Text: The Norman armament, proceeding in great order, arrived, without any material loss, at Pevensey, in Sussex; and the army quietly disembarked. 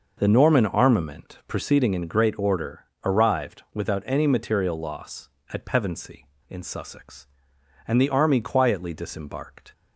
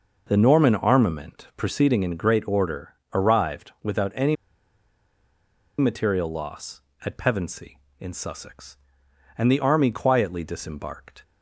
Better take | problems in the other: first | pauses between "any" and "material"; strong; at 4.3 s; 1.4 s long

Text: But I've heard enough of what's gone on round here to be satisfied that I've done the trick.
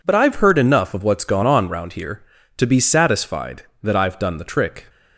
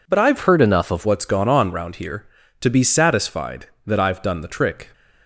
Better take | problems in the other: first | changes voice from "heard" to "of"; from 0.4 to 1.0 s; 0.6 s long

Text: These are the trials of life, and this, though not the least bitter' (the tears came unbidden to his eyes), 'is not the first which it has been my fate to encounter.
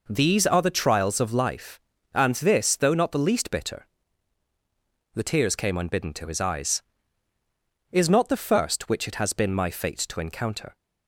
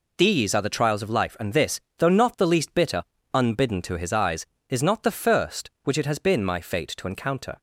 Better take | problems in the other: first | skips "the tears came"; at 3.1 s

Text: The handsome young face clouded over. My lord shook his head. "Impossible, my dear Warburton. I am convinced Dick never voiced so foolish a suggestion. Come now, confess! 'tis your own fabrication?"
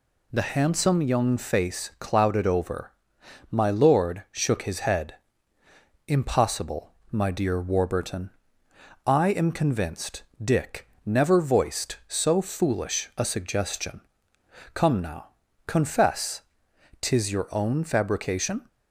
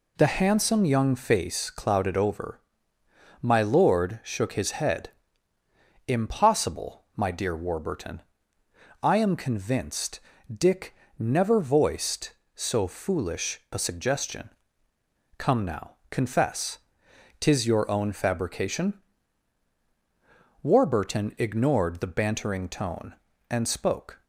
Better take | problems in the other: first | pauses between "convinced" and "Dick"; slight; at 10.1 s; 0.36 s long; slight in the first // pauses between "Dick" and "never"; slight; at 10.9 s; 0.24 s long; slight in the first // goes on to say "Warburton ignored the bantering tone and spoke"; strong; from 20.6 s on; 3.6 s long

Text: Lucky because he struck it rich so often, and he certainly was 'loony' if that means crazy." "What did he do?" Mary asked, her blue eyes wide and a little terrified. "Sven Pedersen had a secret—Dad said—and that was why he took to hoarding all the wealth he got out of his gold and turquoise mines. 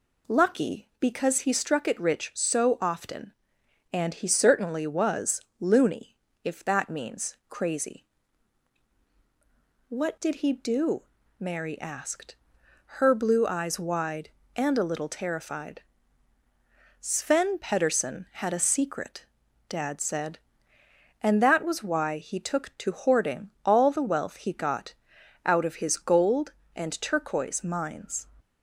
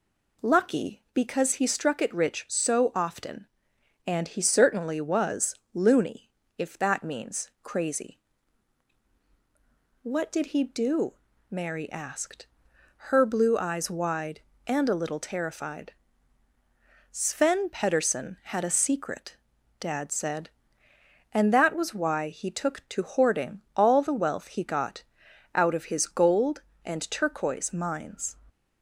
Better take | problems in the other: neither | pauses between "was" and "loony"; slight; the same in both // pauses between "loony" and "if"; slight; the same in both // pauses between "got" and "out"; noticeable; the same in both

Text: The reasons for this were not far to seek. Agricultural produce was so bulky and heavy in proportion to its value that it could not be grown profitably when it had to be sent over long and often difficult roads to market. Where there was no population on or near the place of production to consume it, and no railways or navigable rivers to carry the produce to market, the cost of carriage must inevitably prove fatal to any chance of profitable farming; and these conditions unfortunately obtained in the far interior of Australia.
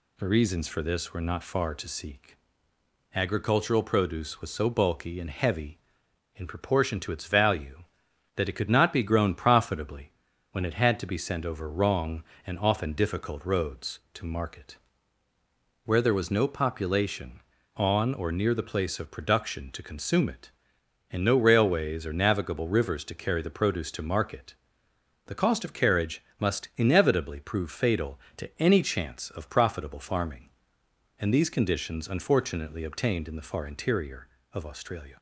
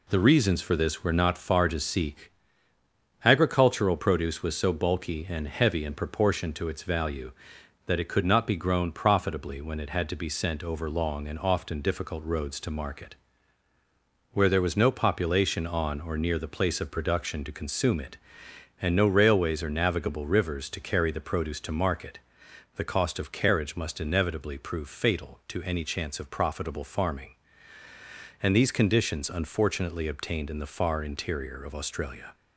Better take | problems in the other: second | pauses between "profitably" and "when"; at 10.1 s; 0.40 s long // says "wrong" for "long"; at 11.6 s // pauses between "carriage" and "must"; slight; at 26.2 s; 0.16 s long

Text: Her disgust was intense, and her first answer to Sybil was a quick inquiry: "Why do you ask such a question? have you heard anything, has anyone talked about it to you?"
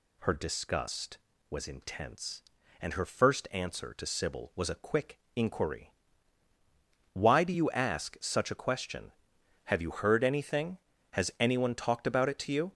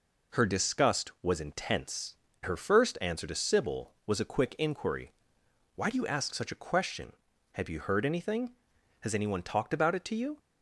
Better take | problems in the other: first | skips "and"; at 2.3 s

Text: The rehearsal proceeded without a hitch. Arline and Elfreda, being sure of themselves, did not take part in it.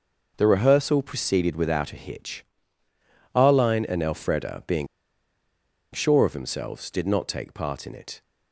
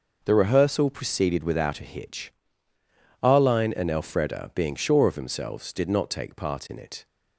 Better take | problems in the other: second | pauses between "being" and "sure"; at 4.8 s; 1.0 s long

